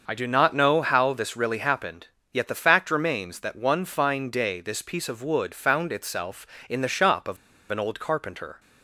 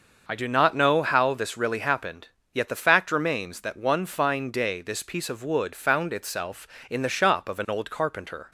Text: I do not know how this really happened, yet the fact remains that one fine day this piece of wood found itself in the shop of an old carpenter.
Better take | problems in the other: second | starts louder than the rest; until 1.0 s; 6 dB; also in the second // pauses between "of" and "an"; slight; at 7.3 s; 0.35 s long

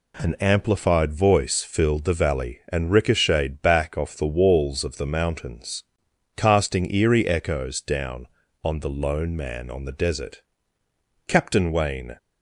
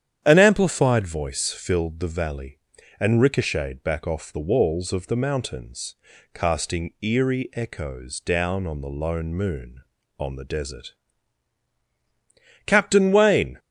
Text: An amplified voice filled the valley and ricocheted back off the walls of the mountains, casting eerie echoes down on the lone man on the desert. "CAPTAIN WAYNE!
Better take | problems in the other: first | starts louder than the rest; strong; until 1.2 s; 9.5 dB // says "moon" for "man"; at 9.3 s

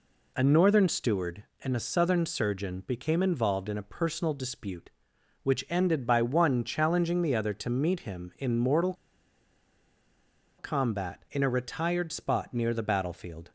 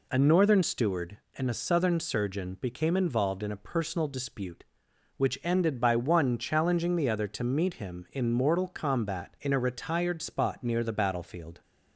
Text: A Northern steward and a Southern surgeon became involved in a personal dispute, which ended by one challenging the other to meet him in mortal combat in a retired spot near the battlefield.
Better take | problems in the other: second | pauses between "mortal" and "combat"; strong; at 8.9 s; 1.6 s long

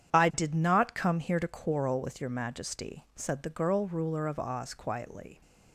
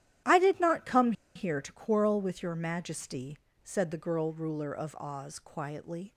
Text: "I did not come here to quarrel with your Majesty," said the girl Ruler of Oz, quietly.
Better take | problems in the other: first | starts louder than the rest; strong; until 1.5 s; 11.5 dB; strong in the first // pauses between "come" and "here"; slight; at 1.1 s; 0.23 s long

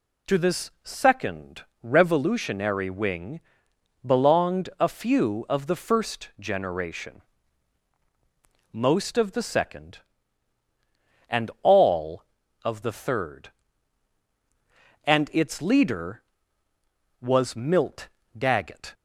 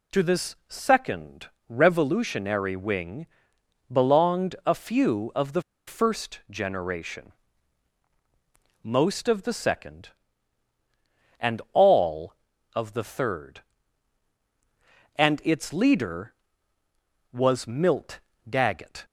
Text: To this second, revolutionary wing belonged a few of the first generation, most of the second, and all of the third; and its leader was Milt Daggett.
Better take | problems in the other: first | pauses between "wing" and "belonged"; noticeable; at 3.2 s; 0.66 s long; noticeable in the first // pauses between "the" and "first"; slight; at 5.6 s; 0.27 s long // pauses between "Milt" and "Daggett"; slight; at 18.1 s; 0.30 s long; slight in the first

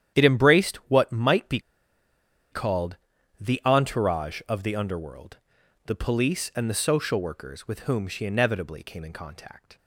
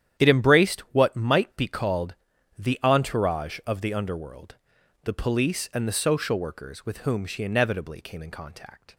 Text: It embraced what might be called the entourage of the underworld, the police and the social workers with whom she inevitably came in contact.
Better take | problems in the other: second | starts louder than the rest; strong; until 1.2 s; 10 dB; strong in the second // pauses between "be" and "called"; noticeable; at 1.5 s; 0.92 s long // pauses between "called" and "the"; at 2.9 s; 0.42 s long; also in the second

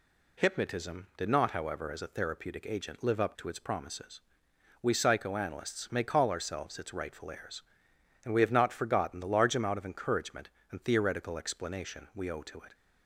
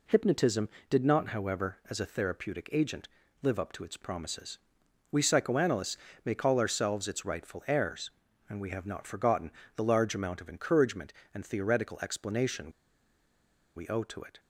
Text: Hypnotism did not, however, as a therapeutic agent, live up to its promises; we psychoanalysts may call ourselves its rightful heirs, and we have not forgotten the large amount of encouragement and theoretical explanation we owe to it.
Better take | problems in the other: first | pauses between "psychoanalysts" and "may"; slight; at 5.9 s; 0.26 s long // pauses between "forgotten" and "the"; slight; at 9.5 s; 0.24 s long // pauses between "explanation" and "we"; at 12.7 s; 1.0 s long

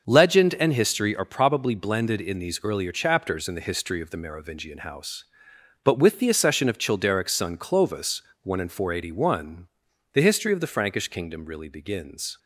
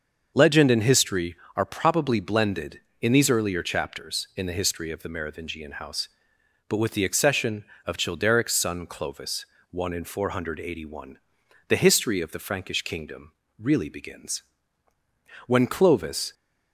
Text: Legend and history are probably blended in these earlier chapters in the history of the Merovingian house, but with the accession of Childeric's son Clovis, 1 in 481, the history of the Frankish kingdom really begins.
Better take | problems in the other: first | starts louder than the rest; until 1.3 s; 6.5 dB; also in the first // pauses between "kingdom" and "really"; slight; at 13.3 s; 0.26 s long // goes on to say "When Clovis"; noticeable; from 15.4 s on; 0.86 s long

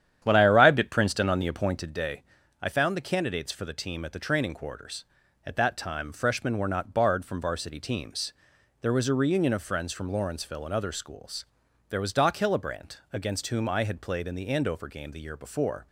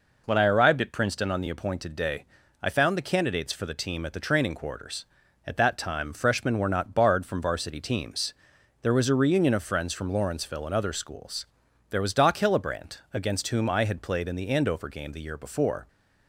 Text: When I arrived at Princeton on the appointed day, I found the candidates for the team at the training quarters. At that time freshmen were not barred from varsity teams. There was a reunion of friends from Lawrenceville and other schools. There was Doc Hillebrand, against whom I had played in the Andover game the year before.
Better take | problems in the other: second | starts louder than the rest; strong; until 2.0 s; 10 dB

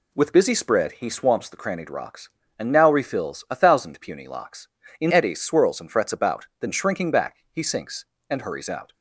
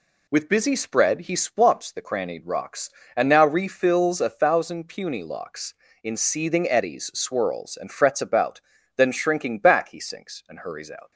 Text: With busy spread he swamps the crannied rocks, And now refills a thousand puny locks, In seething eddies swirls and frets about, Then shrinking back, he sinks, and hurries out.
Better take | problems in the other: second | skips "seething"; at 5.1 s

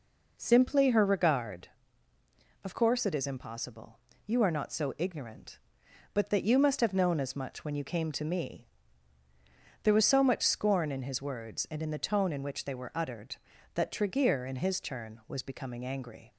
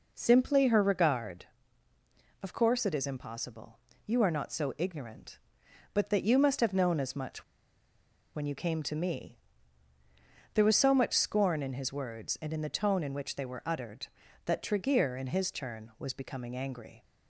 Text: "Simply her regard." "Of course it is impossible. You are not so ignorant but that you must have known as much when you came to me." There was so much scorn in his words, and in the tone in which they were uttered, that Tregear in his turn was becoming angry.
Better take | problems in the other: first | pauses between "much" and "when"; noticeable; at 7.4 s; 0.91 s long

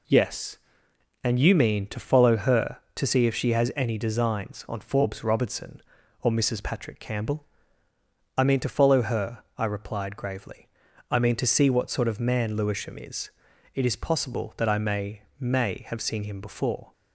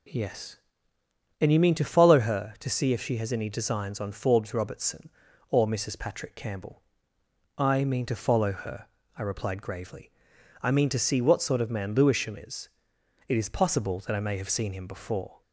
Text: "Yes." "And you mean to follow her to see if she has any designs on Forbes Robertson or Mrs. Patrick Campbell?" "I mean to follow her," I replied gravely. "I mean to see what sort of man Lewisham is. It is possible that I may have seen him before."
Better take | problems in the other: second | says "may" twice; at 15.3 s

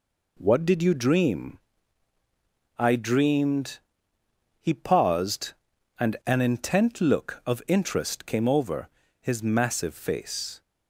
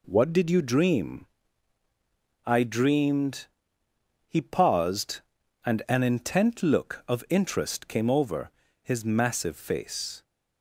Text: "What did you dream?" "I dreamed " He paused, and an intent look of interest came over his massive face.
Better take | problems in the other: neither | pauses between "over" and "his"; slight; the same in both

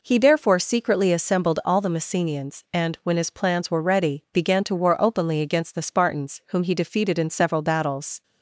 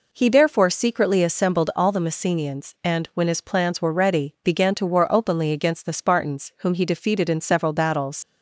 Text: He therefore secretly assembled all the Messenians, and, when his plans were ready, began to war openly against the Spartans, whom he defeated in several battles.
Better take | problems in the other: first | leaves "battles" unfinished; at 8.2 s; 110 ms

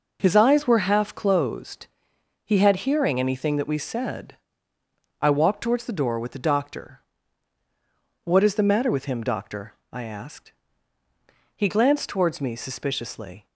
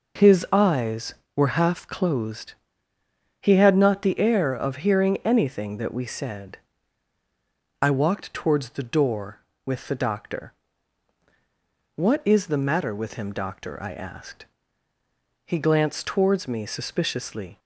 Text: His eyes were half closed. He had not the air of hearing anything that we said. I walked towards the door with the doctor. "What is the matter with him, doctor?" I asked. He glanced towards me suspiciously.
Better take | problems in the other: second | skips "not the air of"; at 2.8 s

